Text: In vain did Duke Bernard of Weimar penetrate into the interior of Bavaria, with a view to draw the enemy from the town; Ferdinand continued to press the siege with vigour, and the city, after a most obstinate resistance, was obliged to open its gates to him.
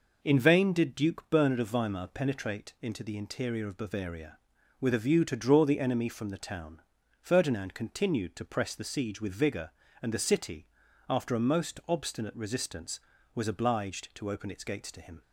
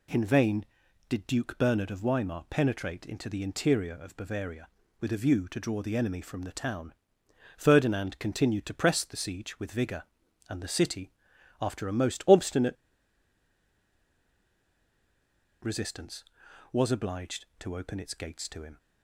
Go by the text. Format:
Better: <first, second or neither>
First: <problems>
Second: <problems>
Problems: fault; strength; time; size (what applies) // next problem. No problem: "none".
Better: first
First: none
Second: pauses between "obstinate" and "resistance"; strong; at 12.7 s; 2.8 s long